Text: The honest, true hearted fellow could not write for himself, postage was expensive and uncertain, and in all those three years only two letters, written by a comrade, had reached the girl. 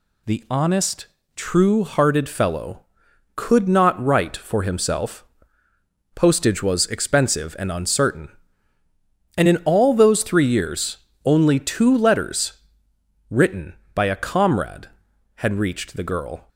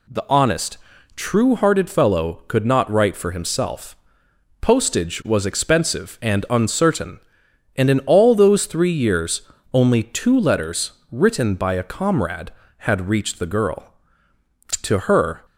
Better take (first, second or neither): first